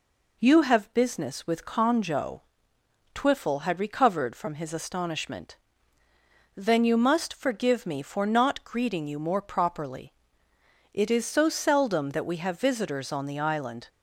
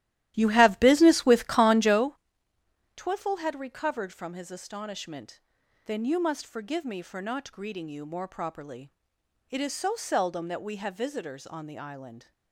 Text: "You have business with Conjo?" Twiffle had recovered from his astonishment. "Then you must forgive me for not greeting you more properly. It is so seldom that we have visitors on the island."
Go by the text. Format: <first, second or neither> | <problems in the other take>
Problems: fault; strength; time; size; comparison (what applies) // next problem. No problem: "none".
first | starts louder than the rest; strong; until 2.2 s; 13.5 dB